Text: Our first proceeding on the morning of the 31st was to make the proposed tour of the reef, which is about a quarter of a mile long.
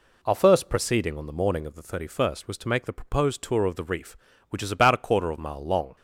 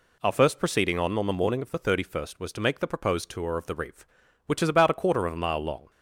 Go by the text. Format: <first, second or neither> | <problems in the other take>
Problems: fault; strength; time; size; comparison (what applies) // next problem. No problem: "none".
first | says "on" twice; at 1.1 s